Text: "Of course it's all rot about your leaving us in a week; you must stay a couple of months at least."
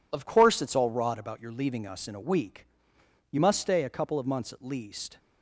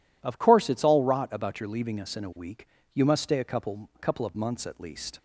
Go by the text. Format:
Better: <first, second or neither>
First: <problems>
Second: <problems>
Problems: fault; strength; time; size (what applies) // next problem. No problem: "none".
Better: first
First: none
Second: says "couple" twice; at 4.0 s